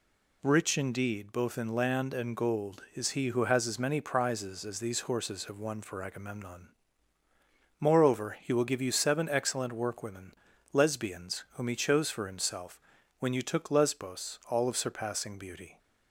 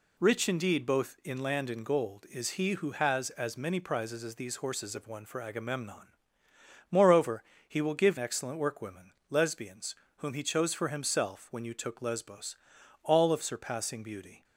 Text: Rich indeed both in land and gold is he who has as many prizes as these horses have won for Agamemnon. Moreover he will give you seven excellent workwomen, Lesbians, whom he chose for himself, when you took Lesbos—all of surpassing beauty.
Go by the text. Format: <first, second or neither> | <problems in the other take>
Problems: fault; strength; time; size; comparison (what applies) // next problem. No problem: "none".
first | pauses between "Moreover" and "he"; slight; at 7.4 s; 0.26 s long // skips "you seven"; at 8.1 s